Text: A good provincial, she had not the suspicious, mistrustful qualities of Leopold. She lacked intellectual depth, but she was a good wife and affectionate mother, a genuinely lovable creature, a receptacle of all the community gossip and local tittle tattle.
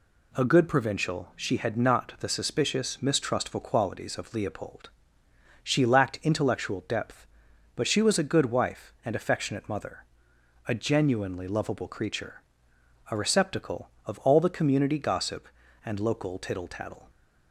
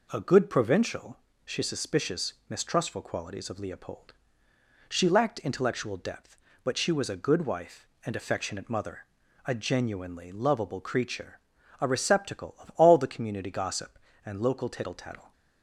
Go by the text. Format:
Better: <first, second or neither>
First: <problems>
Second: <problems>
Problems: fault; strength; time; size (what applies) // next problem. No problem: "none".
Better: first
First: none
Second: skips "had not the"; at 1.6 s